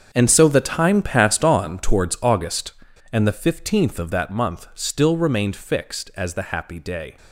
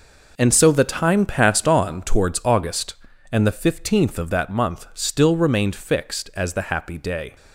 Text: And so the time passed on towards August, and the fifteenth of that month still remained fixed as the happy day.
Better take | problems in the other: second | gets quieter; strong; throughout; 13.5 dB

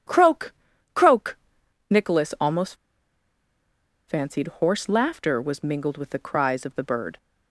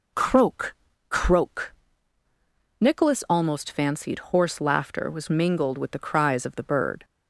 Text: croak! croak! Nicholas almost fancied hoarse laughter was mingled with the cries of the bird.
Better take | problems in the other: second | pauses between "almost" and "fancied"; strong; at 2.7 s; 1.3 s long

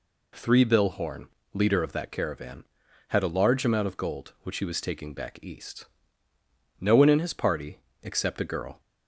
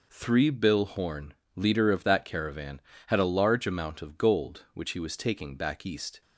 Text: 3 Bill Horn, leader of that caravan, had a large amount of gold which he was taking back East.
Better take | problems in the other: second | goes on to say "No one in his party except a girl"; strong; from 6.7 s on; 2.0 s long

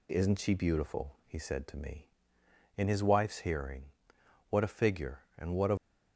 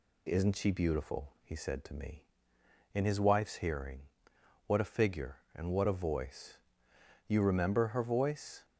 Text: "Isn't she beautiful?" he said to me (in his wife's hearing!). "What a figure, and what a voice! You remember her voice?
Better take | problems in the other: second | stops before "voice You remember her voice"; at 5.7 s

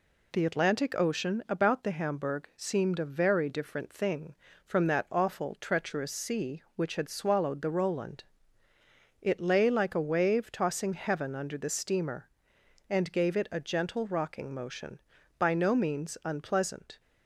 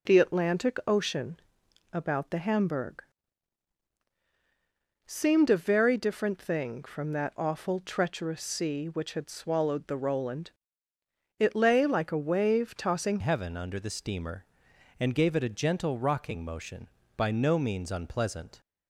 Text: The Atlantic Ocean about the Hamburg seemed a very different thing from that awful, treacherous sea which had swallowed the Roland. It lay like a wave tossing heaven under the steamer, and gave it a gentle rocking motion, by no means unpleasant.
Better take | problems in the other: first | pauses between "Ocean" and "about"; noticeable; at 1.4 s; 0.52 s long // pauses between "Hamburg" and "seemed"; strong; at 3.0 s; 2.0 s long // changes voice at "heaven"; from 13.2 s on; 5.3 s long

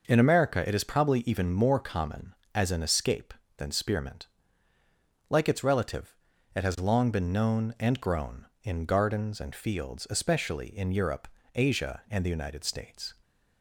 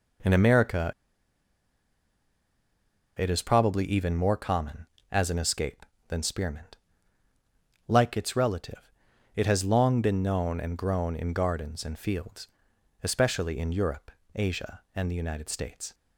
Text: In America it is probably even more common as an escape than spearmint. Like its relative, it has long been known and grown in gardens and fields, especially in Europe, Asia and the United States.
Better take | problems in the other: first | pauses between "America" and "it"; strong; at 0.9 s; 2.2 s long

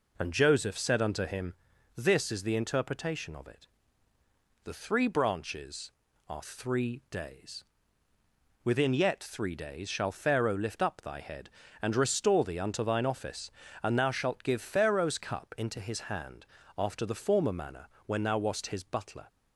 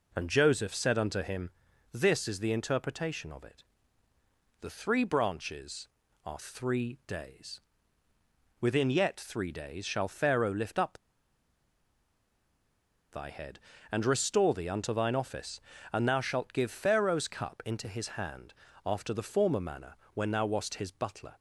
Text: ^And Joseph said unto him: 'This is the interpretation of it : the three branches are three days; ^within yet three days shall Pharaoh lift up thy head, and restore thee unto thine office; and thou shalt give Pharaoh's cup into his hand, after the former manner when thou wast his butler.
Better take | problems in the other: first | pauses between "up" and "thy"; strong; at 10.9 s; 2.1 s long // pauses between "manner" and "when"; slight; at 19.9 s; 0.20 s long; slight in the first

